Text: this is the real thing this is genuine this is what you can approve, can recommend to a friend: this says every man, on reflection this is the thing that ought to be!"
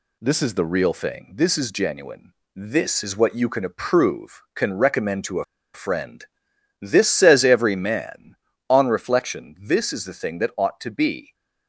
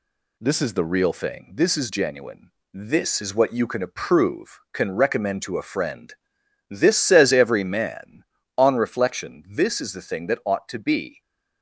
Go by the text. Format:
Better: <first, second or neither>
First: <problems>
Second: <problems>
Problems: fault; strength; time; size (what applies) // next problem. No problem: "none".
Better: second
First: pauses between "genuine" and "this"; slight; at 2.3 s; 0.22 s long // pauses between "a" and "friend"; slight; at 5.4 s; 0.29 s long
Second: pauses between "genuine" and "this"; slight; at 2.4 s; 0.22 s long